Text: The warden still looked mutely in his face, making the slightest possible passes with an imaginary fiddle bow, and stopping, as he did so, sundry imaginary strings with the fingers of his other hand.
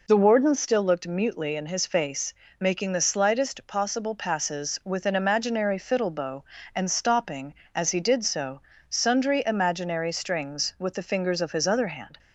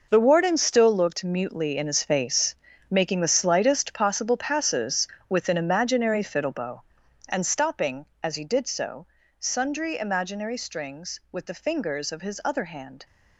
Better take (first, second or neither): first